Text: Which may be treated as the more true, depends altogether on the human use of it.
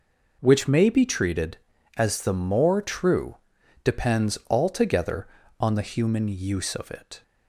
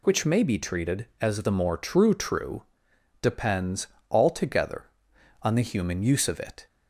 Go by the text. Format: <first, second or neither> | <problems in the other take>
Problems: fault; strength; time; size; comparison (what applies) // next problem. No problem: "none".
first | says "true" twice; at 2.1 s // pauses between "depends" and "altogether"; slight; at 3.8 s; 0.24 s long